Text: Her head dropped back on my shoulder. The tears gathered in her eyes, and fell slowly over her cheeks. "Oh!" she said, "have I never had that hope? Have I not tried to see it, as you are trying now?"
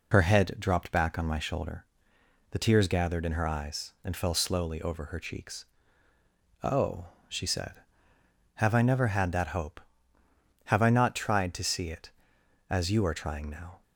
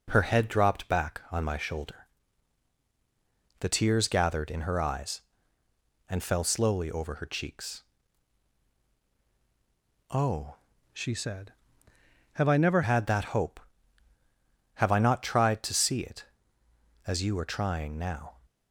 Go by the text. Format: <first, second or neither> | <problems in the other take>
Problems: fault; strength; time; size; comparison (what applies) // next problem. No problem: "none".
first | changes voice from "she" to "never"; from 10.9 to 12.8 s; 1.9 s long